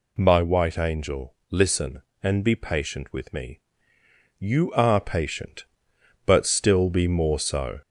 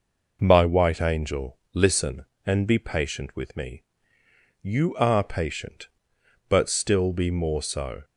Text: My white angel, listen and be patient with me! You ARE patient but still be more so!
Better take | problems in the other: second | gets louder; throughout; 3.5 dB

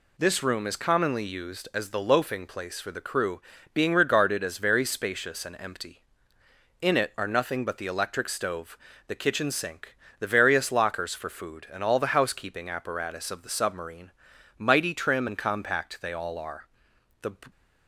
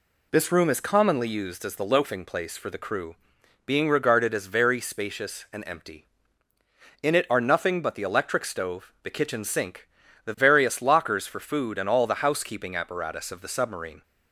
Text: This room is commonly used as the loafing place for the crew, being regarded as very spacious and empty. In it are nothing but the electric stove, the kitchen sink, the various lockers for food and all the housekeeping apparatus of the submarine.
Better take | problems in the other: second | goes on to say "Mighty trim and compact they all are The"; strong; from 14.5 s on; 2.7 s long

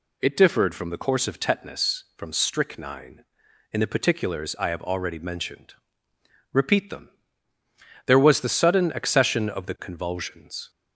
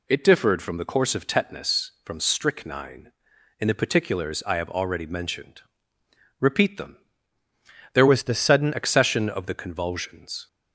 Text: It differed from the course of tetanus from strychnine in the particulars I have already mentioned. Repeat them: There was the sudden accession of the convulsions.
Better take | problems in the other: first | changes voice from "was" to "sudden"; from 8.0 to 8.7 s; 0.7 s long

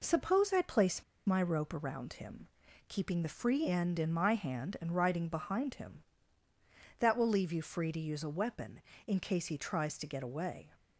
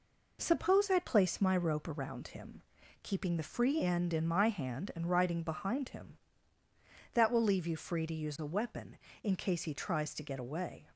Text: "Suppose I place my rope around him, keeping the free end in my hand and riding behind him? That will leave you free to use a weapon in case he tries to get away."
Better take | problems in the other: second | pauses between "place" and "my"; slight; at 1.0 s; 0.24 s long

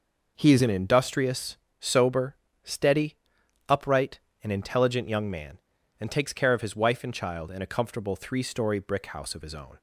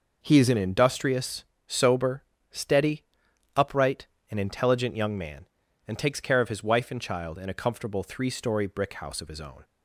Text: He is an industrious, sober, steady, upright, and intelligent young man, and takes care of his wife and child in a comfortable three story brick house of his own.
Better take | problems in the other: neither | none

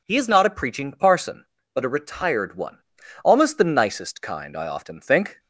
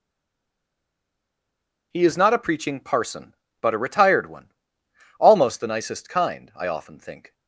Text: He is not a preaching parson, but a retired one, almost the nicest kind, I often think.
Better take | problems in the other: first | stays silent before the first word; noticeable; until 1.9 s; 1.9 s long

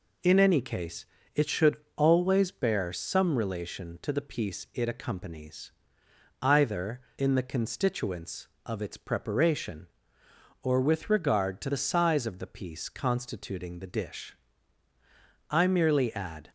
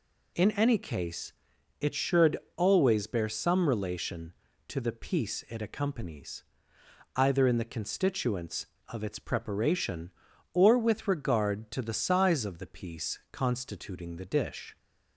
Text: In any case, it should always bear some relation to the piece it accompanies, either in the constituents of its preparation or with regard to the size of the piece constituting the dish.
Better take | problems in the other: second | pauses between "should" and "always"; slight; at 1.7 s; 0.17 s long; slight in the second // goes on to say "I merely add"; noticeable; from 15.5 s on; 0.98 s long

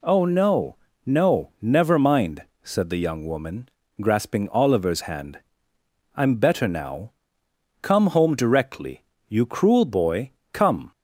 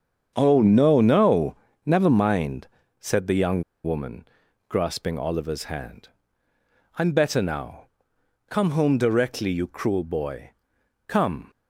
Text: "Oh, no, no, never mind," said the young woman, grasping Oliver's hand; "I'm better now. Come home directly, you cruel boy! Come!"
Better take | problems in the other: first | starts louder than the rest; strong; until 1.3 s; 7.5 dB // pauses between "young" and "woman"; slight; at 3.6 s; 0.21 s long

